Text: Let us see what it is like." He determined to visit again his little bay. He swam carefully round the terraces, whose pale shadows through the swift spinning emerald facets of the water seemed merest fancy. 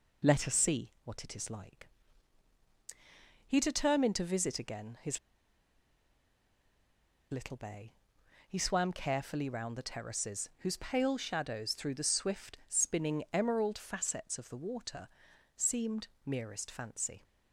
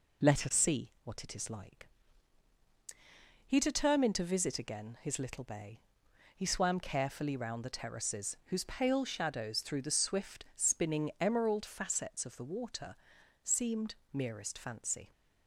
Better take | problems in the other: second | pauses between "his" and "little"; strong; at 5.1 s; 2.1 s long // pauses between "water" and "seemed"; noticeable; at 15.0 s; 0.48 s long; noticeable in the second // pauses between "seemed" and "merest"; slight; at 16.0 s; 0.18 s long; slight in the second

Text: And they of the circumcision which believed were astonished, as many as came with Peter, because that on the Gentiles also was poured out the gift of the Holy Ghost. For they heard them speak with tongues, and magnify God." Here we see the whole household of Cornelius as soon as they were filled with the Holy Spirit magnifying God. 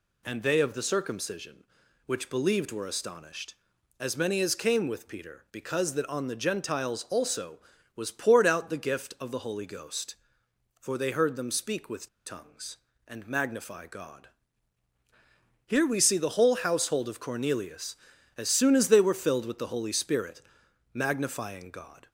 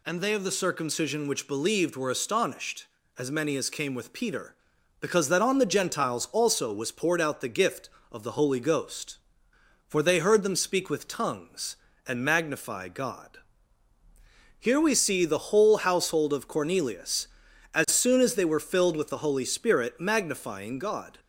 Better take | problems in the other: second | pauses between "with" and "tongues"; slight; at 12.0 s; 0.18 s long // pauses between "Spirit" and "magnifying"; noticeable; at 20.4 s; 0.50 s long

